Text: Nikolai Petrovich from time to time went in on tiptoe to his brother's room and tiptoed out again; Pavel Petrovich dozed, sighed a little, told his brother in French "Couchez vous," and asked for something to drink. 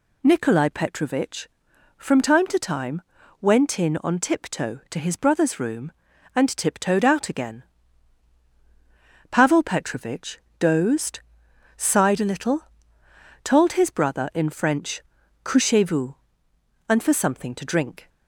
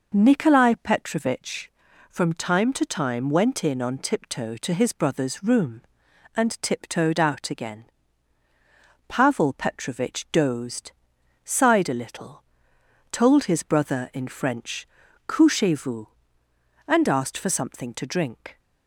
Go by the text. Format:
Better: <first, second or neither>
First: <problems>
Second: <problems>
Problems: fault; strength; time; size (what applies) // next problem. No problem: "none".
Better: second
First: pauses between "time" and "went"; at 3.0 s; 0.40 s long // pauses between "Petrovich" and "dozed"; slight; at 10.3 s; 0.20 s long // pauses between "French" and "Couchez"; at 15.0 s; 0.42 s long // skips "asked"; at 17.0 s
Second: pauses between "French" and "Couchez"; at 14.8 s; 0.40 s long